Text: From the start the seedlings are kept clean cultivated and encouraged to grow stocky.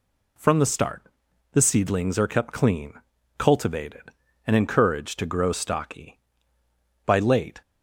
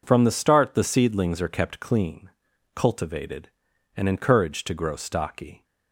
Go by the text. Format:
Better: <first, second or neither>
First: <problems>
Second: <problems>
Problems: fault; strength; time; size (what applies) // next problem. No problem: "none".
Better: second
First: pauses between "start" and "the"; noticeable; at 1.0 s; 0.52 s long // pauses between "clean" and "cultivated"; at 2.9 s; 0.44 s long // goes on to say "By late"; from 7.0 s on; 0.54 s long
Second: pauses between "clean" and "cultivated"; noticeable; at 2.2 s; 0.46 s long